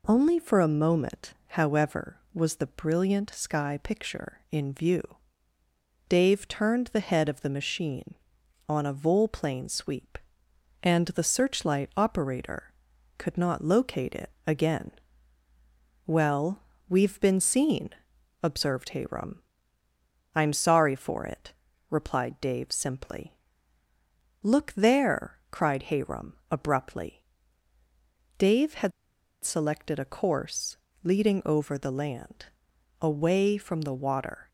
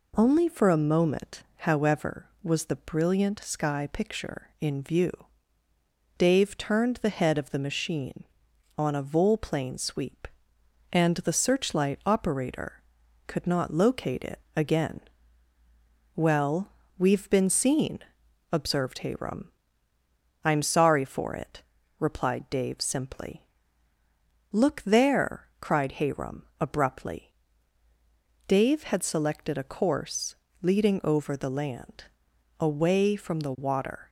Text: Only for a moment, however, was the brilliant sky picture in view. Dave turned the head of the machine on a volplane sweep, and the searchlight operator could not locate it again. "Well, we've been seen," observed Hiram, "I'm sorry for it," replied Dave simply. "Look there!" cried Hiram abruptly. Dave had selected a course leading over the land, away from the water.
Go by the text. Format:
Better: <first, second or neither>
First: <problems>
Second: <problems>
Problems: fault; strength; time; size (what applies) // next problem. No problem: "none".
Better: second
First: pauses between "it" and "again"; slight; at 14.2 s; 0.16 s long // pauses between "had" and "selected"; noticeable; at 28.9 s; 0.52 s long // pauses between "course" and "leading"; slight; at 30.7 s; 0.26 s long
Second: pauses between "it" and "again"; slight; at 14.3 s; 0.16 s long // pauses between "course" and "leading"; slight; at 30.3 s; 0.26 s long